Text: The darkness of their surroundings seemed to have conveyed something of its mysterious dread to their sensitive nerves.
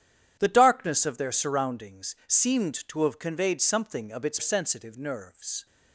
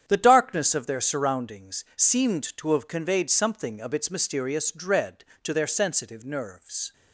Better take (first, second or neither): second